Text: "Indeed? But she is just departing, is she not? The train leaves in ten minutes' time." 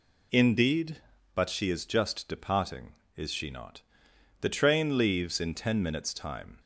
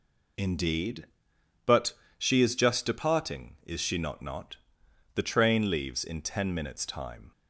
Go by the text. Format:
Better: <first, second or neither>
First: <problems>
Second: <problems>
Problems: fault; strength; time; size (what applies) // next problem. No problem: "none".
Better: first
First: none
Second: pauses between "But" and "she"; slight; at 1.9 s; 0.24 s long // says "not" twice; at 4.2 s